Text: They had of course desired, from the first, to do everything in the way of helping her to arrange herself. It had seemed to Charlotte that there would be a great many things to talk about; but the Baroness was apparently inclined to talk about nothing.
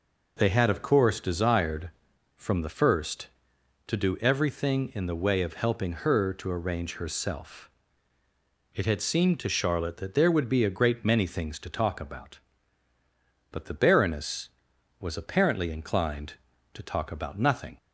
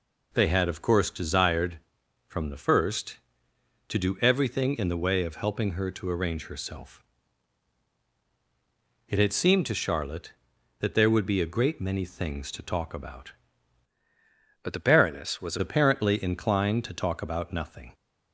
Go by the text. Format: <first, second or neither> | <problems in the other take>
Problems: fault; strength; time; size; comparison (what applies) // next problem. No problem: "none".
first | changes voice from "but" to "was"; from 14.6 to 15.5 s; 0.9 s long